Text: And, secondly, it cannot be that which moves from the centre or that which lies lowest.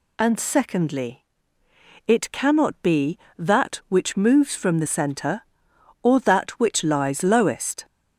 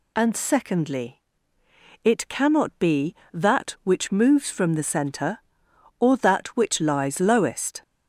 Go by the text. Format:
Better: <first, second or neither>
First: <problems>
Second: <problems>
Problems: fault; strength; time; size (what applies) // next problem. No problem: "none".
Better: neither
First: none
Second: none